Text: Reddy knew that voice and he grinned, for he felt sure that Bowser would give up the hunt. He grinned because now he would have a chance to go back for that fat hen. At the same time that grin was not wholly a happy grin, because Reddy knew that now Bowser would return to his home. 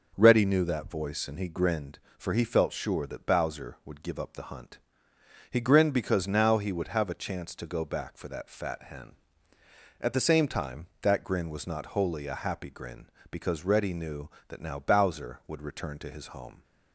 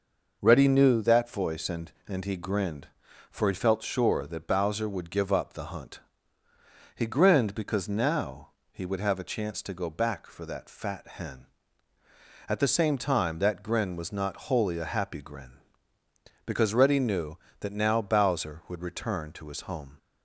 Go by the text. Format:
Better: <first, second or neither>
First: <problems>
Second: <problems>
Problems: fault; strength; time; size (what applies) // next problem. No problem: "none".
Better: first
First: none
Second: says "and" twice; at 2.0 s // pauses between "now" and "he"; slight; at 8.4 s; 0.22 s long